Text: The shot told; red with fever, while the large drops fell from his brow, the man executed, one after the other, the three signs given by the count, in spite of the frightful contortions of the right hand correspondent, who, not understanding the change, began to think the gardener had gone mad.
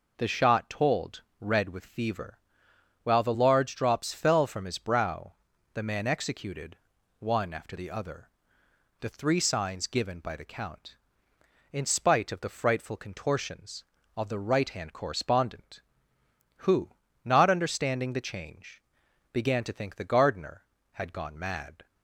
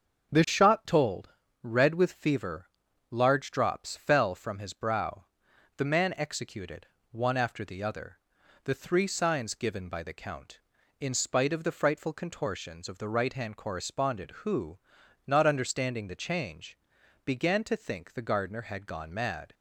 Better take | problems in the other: first | starts louder than the rest; until 1.7 s; 6.5 dB // skips "while the"; at 2.8 s

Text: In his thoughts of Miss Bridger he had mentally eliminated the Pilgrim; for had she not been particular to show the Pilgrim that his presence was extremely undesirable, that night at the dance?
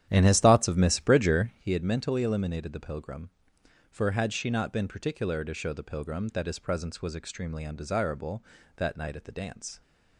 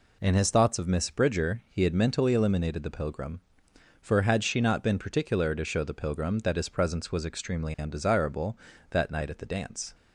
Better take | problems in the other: second | starts louder than the rest; strong; until 1.7 s; 10.5 dB

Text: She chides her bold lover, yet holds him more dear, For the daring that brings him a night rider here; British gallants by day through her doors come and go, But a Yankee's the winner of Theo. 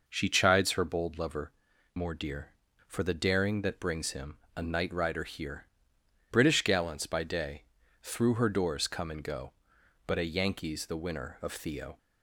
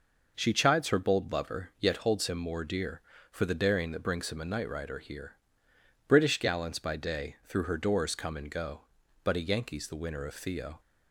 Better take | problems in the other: second | skips "yet holds him"; at 1.7 s // pauses between "him" and "a"; slight; at 4.3 s; 0.18 s long // pauses between "day" and "through"; at 7.6 s; 0.38 s long

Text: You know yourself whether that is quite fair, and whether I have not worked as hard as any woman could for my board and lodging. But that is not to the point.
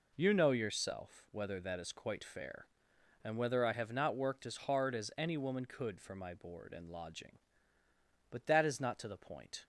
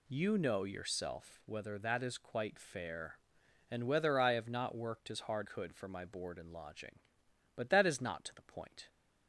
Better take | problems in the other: first | skips "as any woman"; at 5.4 s

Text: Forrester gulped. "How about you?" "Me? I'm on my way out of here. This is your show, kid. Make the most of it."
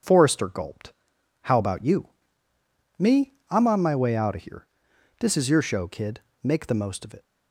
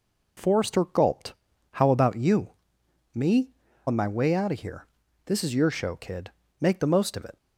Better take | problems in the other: first | skips "I'm"; at 3.6 s

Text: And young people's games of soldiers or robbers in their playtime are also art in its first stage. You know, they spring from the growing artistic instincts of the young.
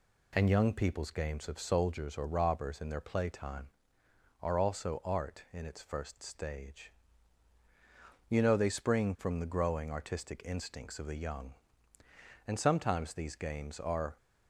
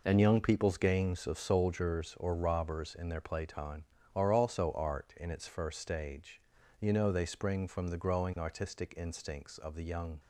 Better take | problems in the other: second | goes on to say "And sometimes these games are"; strong; from 12.4 s on; 1.7 s long

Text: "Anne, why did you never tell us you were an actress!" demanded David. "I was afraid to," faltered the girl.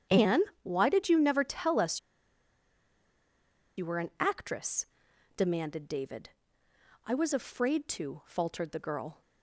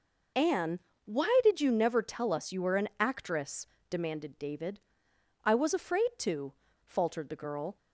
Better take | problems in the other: second | starts louder than the rest; strong; until 1.3 s; 9 dB // pauses between "us" and "you"; strong; at 1.9 s; 1.7 s long

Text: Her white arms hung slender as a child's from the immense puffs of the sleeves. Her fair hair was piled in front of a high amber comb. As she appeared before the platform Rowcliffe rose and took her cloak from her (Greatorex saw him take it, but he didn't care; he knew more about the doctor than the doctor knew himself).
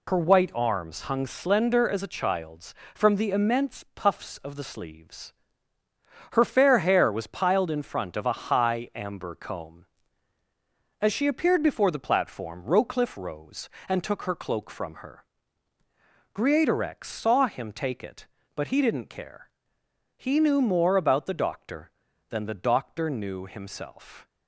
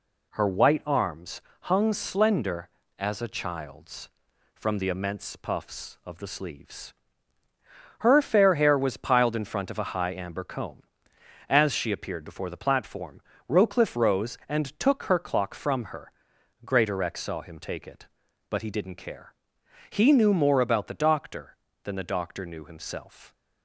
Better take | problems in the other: first | pauses between "arms" and "hung"; slight; at 1.4 s; 0.20 s long // pauses between "platform" and "Rowcliffe"; slight; at 13.2 s; 0.26 s long // says "clock" for "cloak"; at 15.1 s

